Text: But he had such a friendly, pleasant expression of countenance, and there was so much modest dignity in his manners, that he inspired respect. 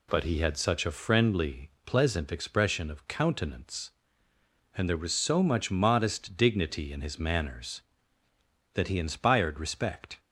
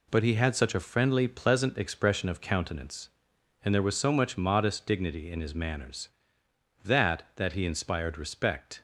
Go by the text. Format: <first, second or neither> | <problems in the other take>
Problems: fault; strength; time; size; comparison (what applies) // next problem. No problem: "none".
first | says "that" twice; at 7.3 s